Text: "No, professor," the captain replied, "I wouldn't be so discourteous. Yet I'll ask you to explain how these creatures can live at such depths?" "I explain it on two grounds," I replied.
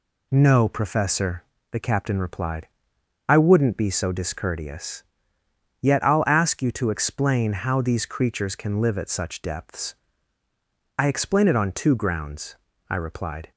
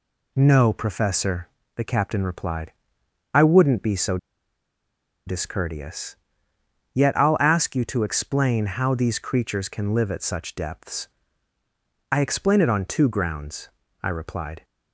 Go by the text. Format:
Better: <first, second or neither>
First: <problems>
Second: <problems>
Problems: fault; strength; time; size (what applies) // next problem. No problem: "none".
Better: first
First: none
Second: pauses between "so" and "discourteous"; at 4.1 s; 1.0 s long